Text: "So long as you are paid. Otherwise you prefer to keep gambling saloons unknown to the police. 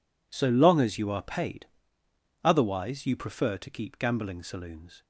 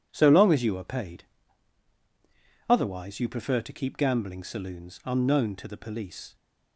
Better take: second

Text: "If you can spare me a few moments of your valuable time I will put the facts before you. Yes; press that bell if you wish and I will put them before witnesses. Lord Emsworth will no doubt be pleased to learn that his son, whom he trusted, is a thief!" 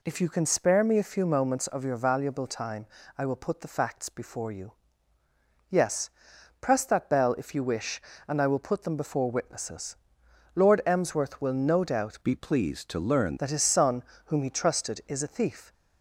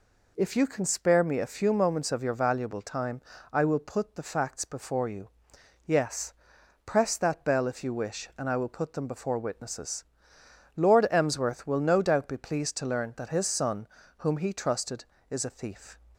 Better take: second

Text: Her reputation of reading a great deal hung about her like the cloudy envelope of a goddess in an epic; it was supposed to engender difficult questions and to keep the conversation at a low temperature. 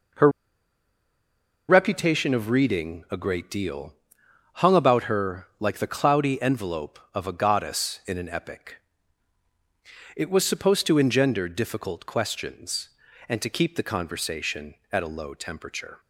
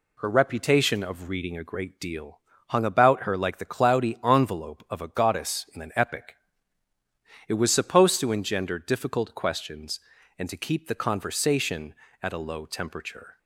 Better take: second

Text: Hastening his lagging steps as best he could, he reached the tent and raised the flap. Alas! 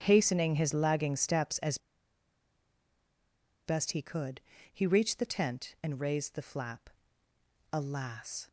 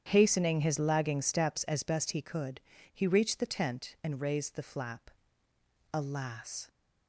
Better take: second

